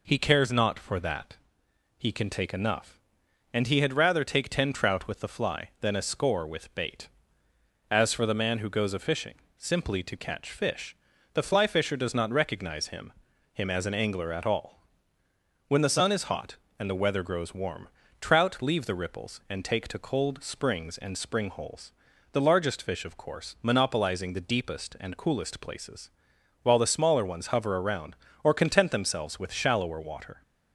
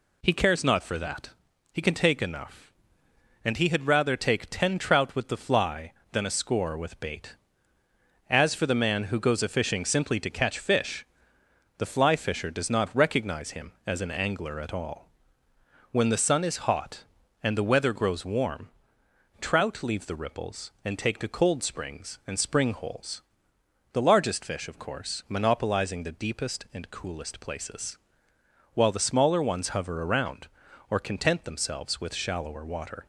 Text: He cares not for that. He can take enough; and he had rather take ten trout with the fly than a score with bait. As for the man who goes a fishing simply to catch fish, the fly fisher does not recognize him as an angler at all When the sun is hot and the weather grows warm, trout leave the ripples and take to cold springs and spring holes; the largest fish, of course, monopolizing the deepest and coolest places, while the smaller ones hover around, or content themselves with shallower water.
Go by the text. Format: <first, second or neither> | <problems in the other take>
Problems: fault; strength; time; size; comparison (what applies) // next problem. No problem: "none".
second | pauses between "fishing" and "simply"; slight; at 9.3 s; 0.24 s long // says "him" twice; at 13.5 s // pauses between "all" and "When"; noticeable; at 14.7 s; 0.88 s long; noticeable in the second